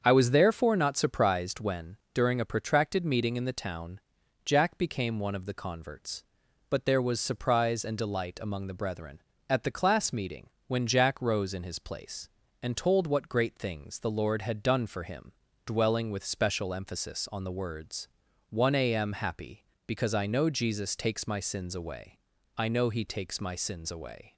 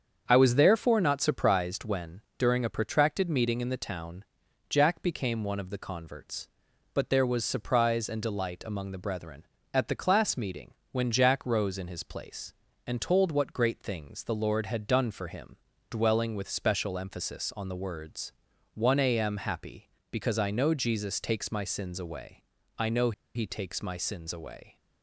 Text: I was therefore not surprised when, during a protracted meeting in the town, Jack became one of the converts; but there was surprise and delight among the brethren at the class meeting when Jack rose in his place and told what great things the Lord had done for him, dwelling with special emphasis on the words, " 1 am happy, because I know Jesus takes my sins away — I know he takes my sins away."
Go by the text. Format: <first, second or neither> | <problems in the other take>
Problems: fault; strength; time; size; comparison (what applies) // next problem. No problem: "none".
first | starts louder than the rest; strong; until 1.2 s; 7 dB; strong in the first // pauses between "meeting" and "when"; slight; at 10.7 s; 0.16 s long; slight in the first // pauses between "know" and "he"; slight; at 23.1 s; 0.23 s long